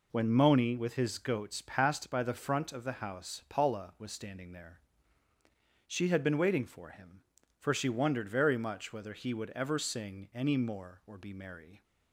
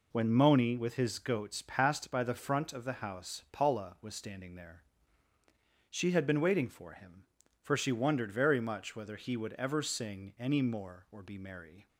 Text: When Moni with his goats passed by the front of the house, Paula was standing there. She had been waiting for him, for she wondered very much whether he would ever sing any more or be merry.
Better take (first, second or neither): neither